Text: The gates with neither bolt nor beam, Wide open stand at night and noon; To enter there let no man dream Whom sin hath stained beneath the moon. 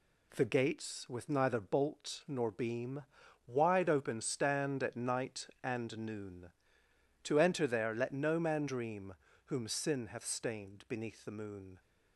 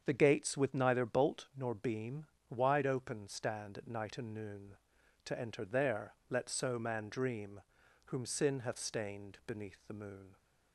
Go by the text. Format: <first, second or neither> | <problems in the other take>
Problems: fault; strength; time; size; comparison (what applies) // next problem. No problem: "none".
first | starts louder than the rest; strong; until 1.0 s; 7.5 dB // says "so" for "no"; at 6.5 s // pauses between "dream" and "Whom"; at 7.6 s; 0.44 s long; slight in the first